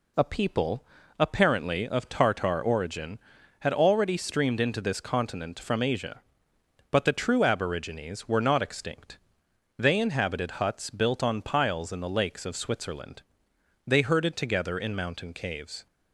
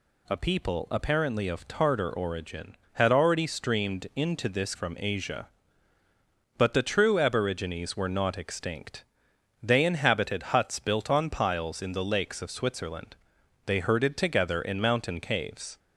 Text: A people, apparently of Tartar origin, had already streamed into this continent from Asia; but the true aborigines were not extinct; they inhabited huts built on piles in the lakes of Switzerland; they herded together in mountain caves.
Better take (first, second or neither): first